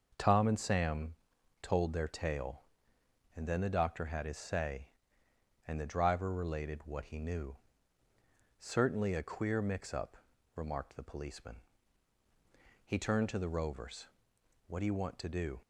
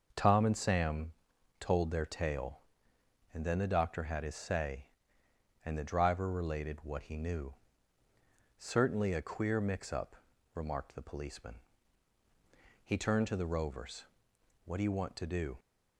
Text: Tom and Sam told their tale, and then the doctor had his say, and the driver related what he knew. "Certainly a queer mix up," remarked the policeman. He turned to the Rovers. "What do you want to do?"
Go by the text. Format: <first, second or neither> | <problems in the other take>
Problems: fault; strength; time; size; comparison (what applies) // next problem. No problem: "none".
neither | starts louder than the rest; noticeable; the same in both // pauses between "Sam" and "told"; noticeable; the same in both